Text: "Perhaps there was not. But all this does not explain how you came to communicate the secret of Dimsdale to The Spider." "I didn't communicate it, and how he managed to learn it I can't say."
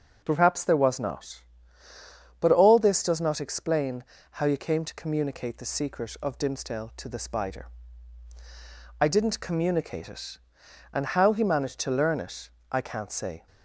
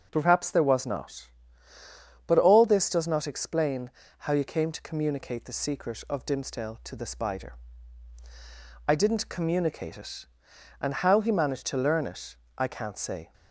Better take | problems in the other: neither | pauses between "explain" and "how"; slight; the same in both // pauses between "it" and "I"; slight; the same in both

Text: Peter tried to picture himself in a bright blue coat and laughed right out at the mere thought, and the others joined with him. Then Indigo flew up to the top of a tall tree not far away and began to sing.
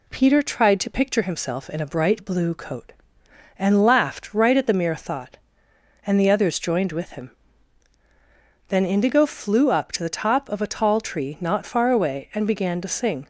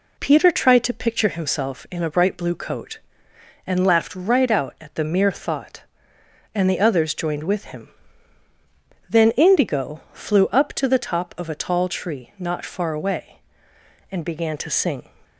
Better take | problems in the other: second | skips "out"; at 4.5 s

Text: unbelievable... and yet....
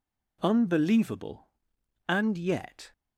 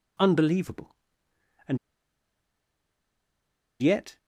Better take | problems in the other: first | pauses between "and" and "yet"; strong; at 1.7 s; 2.0 s long

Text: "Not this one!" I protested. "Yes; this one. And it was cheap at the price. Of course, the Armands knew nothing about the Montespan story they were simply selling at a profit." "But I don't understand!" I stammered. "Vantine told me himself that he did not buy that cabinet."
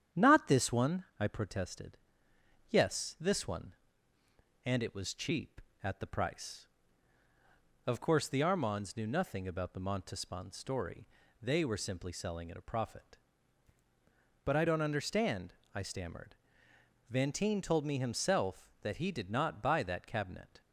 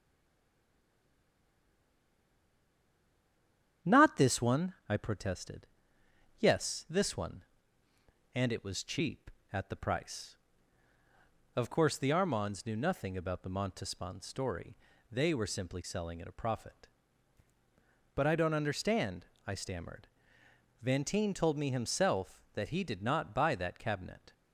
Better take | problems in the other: first | stays silent before the first word; strong; until 3.8 s; 3.8 s long // starts louder than the rest; strong; until 4.9 s; 9 dB; strong in the first // pauses between "story" and "they"; slight; at 14.7 s; 0.34 s long; slight in the first

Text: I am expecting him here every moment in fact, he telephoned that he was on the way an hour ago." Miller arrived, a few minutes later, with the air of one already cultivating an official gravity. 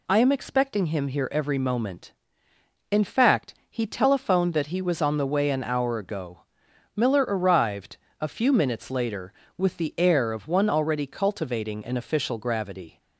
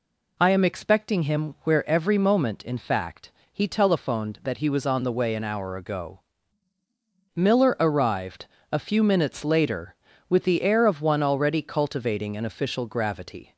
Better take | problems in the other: first | says "where" for "here"; at 1.6 s

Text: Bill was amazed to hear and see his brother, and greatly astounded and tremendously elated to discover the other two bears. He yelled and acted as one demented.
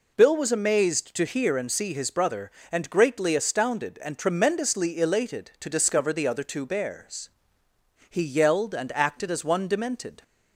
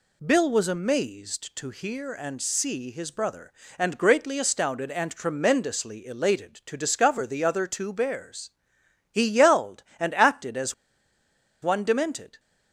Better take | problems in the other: first | pauses between "as" and "one"; noticeable; at 10.7 s; 0.89 s long

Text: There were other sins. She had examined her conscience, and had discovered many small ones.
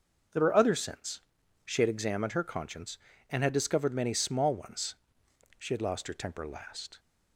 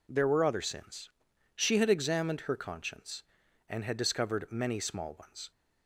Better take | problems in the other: second | starts louder than the rest; noticeable; until 1.7 s; 6 dB // goes on to say "She had lost her temper last"; from 5.5 s on; 1.4 s long

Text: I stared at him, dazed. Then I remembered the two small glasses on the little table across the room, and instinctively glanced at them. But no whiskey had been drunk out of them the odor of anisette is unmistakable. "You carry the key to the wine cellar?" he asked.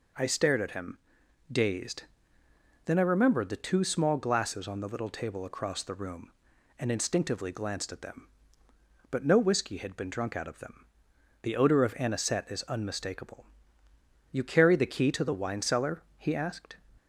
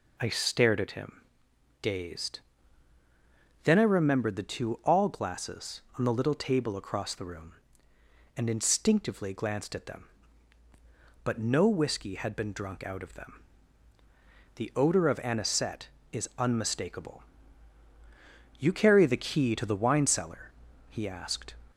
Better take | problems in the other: first | says "all" for "small"; at 4.8 s // pauses between "them" and "the"; at 13.4 s; 1.1 s long; noticeable in the first

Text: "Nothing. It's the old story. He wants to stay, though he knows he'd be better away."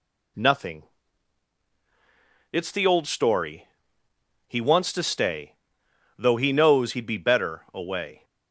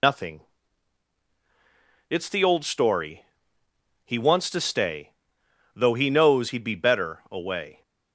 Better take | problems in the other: first | loses the start of "Nothing"; at 0.0 s; 95 ms

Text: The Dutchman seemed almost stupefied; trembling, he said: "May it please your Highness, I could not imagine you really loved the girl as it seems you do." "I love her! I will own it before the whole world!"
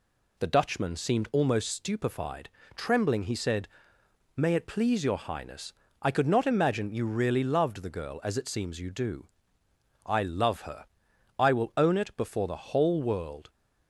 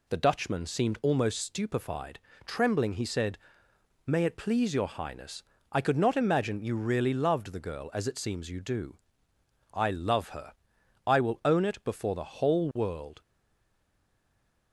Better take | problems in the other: first | stays silent after the last word; noticeable; from 13.2 s on; 1.5 s long

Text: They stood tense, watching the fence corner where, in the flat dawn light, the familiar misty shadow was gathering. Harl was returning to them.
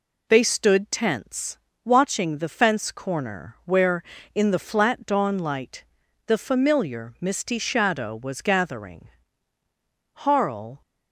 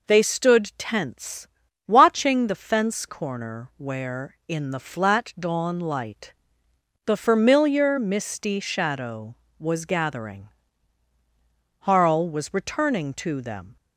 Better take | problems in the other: second | stops before "was returning to them"; at 10.8 s

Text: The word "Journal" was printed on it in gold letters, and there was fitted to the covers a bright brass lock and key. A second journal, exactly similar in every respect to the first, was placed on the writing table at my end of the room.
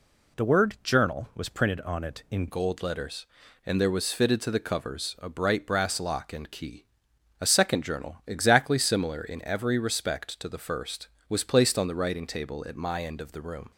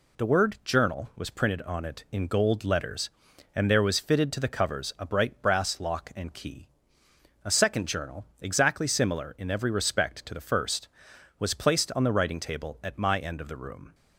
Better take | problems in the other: second | changes voice at "gold"; from 2.4 s on; 11.3 s long

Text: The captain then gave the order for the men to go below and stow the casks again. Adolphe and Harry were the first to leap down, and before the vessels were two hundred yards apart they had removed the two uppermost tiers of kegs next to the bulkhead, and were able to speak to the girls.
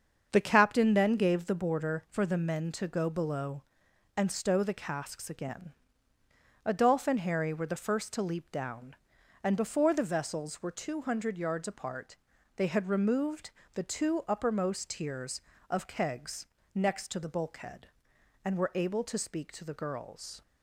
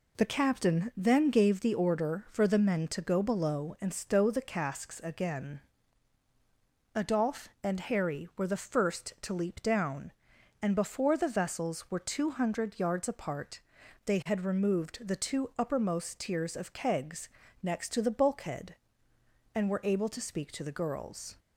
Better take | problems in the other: second | starts louder than the rest; until 1.3 s; 7 dB // says "border" for "order"; at 1.5 s // pauses between "apart" and "they"; at 12.1 s; 0.42 s long; noticeable in the second // pauses between "removed" and "the"; slight; at 13.4 s; 0.24 s long // pauses between "kegs" and "next"; slight; at 16.4 s; 0.30 s long; slight in the second

